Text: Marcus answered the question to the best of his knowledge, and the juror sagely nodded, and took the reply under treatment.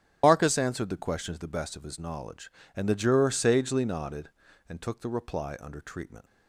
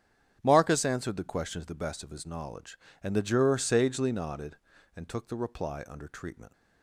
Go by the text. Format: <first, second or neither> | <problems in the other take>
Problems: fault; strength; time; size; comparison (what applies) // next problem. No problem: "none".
second | loses the start of "Marcus"; at 0.2 s; 120 ms // starts louder than the rest; strong; until 1.2 s; 10 dB; strong in the second